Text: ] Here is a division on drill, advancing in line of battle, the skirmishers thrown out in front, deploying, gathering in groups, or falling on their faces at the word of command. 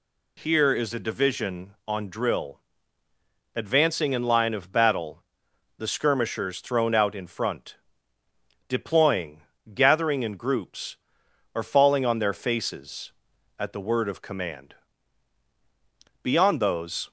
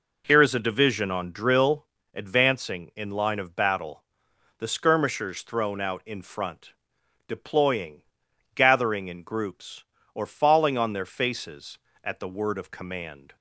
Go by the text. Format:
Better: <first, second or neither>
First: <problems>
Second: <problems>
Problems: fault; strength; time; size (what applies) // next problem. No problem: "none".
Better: second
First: goes on to say "Beyond those"; noticeable; from 16.2 s on; 0.88 s long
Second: none